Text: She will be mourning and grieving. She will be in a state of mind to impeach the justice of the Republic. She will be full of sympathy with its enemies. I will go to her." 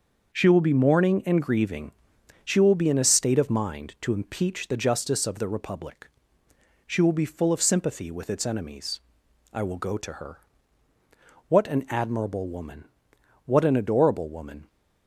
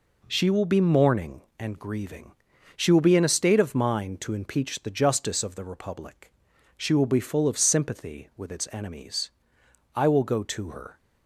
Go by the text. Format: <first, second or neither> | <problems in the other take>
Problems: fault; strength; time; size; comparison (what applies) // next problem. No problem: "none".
second | starts louder than the rest; until 1.3 s; 6.5 dB // goes on to say "What an admirable woman what an adorable woman"; strong; from 11.4 s on; 3.2 s long